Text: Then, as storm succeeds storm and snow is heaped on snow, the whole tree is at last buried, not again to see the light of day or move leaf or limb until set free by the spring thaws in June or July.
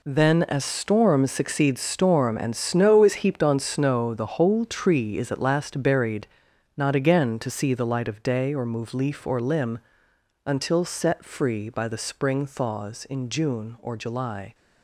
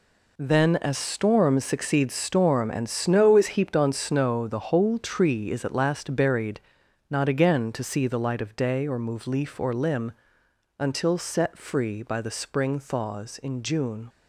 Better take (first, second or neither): first